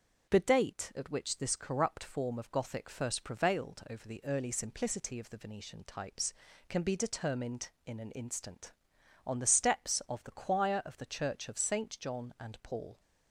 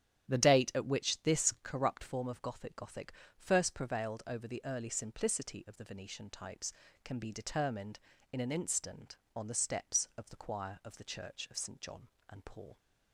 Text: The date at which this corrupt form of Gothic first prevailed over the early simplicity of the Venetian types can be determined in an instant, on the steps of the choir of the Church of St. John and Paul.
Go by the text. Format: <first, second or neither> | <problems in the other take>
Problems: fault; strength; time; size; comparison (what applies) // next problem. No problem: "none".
first | starts louder than the rest; strong; until 1.3 s; 10 dB; also in the first // says "Gothic" twice; at 2.7 s